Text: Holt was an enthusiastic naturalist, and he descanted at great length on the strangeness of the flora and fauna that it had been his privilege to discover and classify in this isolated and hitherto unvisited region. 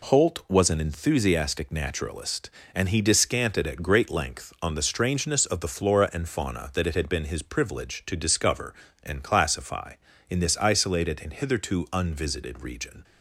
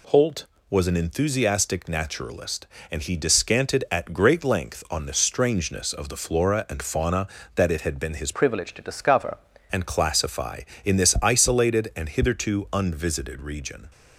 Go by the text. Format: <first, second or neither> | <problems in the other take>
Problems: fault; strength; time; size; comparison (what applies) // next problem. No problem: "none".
first | changes voice from "privilege" to "discover"; from 8.3 to 9.3 s; 1.0 s long